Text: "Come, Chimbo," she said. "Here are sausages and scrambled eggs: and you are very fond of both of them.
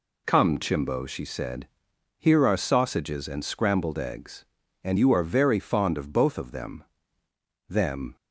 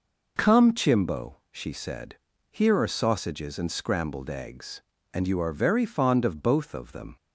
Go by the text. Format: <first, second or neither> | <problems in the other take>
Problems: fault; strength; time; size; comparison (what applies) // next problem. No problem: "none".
second | says "them" twice; at 7.6 s